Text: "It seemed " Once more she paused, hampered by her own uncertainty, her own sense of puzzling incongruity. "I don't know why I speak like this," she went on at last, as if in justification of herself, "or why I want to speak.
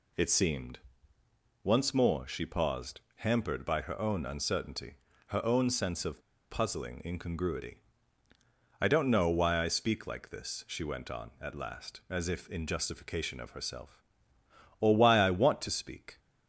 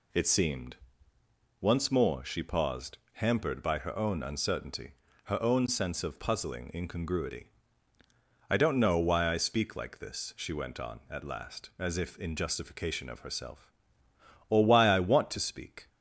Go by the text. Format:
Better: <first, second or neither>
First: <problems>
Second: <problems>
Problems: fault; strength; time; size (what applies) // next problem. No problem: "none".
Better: second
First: pauses between "of" and "puzzling"; slight; at 6.2 s; 0.29 s long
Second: none